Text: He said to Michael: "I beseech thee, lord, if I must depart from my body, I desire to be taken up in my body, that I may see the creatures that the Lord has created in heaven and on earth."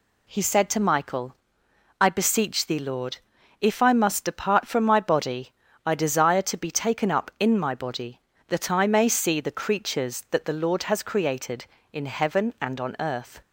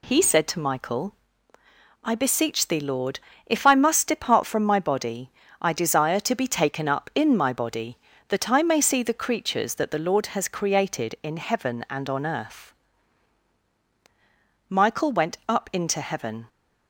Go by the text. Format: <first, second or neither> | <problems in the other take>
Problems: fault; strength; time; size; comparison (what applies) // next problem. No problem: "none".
first | goes on to say "Michael went up into heaven"; strong; from 14.6 s on; 1.8 s long